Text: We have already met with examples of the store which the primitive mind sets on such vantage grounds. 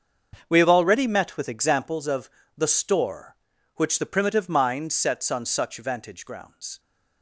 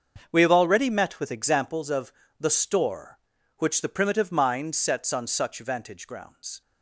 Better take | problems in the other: neither | starts louder than the rest; the same in both // pauses between "of" and "the"; slight; the same in both

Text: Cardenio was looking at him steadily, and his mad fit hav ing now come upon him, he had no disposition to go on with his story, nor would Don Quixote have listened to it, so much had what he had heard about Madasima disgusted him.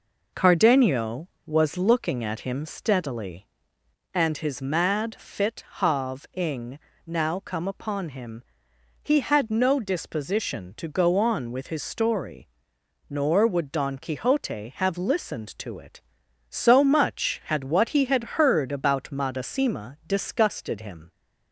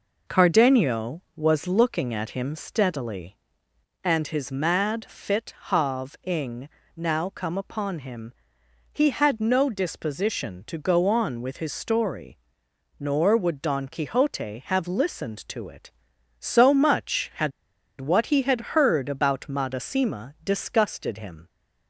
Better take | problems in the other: first | pauses between "ing" and "now"; slight; at 6.6 s; 0.30 s long; slight in the first // pauses between "had" and "what"; noticeable; at 17.5 s; 0.48 s long

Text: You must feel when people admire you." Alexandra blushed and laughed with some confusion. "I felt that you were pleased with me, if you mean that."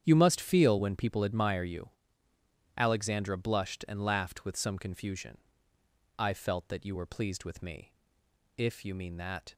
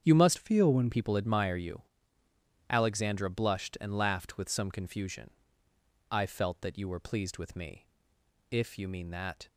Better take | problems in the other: first | starts louder than the rest; strong; until 1.0 s; 8 dB; strong in the first // changes voice from "feel" to "when"; from 0.3 to 0.9 s; 0.6 s long

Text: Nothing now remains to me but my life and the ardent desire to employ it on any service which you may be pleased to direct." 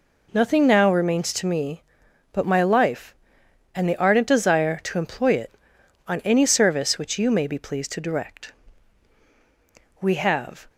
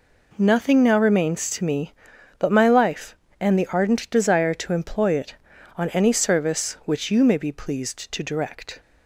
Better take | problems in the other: second | goes on to say "We have"; noticeable; from 10.0 s on; 0.68 s long

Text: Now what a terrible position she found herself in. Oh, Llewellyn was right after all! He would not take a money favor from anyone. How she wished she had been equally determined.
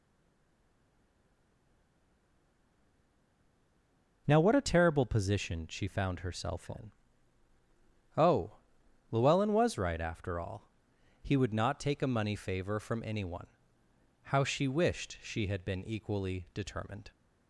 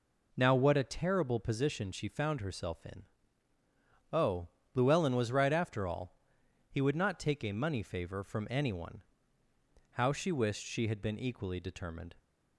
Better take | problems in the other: second | stays silent before the first word; strong; until 4.2 s; 4.2 s long

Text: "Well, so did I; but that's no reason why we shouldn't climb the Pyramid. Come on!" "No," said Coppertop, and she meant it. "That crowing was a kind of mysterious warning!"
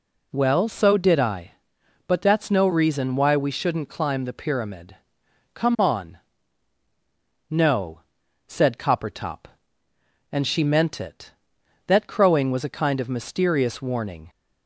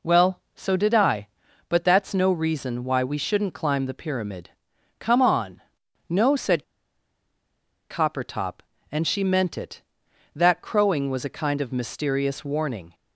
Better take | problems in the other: first | pauses between "said" and "Coppertop"; strong; at 6.6 s; 1.2 s long

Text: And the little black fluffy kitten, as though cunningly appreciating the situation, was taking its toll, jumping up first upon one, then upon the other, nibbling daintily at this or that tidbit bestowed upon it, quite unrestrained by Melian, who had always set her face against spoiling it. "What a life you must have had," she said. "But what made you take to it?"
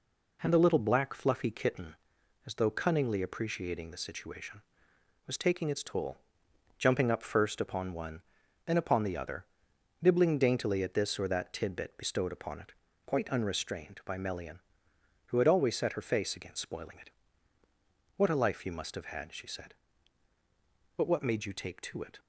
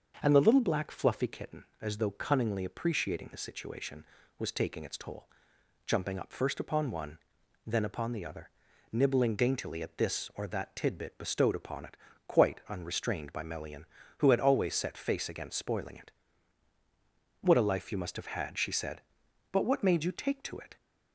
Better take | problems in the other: first | starts louder than the rest; until 1.2 s; 6.5 dB // skips "her"; at 14.9 s

